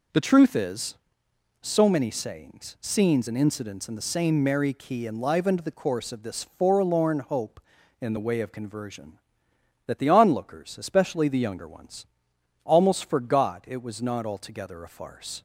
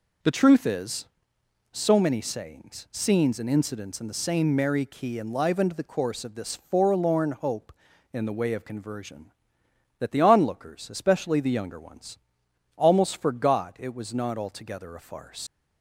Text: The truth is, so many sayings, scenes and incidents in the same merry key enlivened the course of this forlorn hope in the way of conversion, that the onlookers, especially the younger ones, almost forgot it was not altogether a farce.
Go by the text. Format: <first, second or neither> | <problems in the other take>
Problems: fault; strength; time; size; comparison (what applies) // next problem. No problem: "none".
first | leaves "farce" unfinished; at 15.4 s; 70 ms